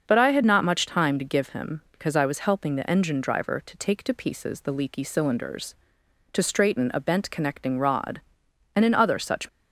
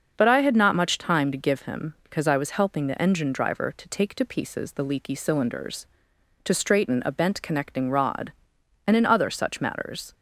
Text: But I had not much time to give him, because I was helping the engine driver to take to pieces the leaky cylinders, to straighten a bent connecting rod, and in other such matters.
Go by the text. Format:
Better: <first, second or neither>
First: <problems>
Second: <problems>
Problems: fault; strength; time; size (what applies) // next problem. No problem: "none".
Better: second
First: starts louder than the rest; until 1.0 s; 6.5 dB // stops before "matters"; at 9.4 s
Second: starts louder than the rest; until 1.1 s; 6.5 dB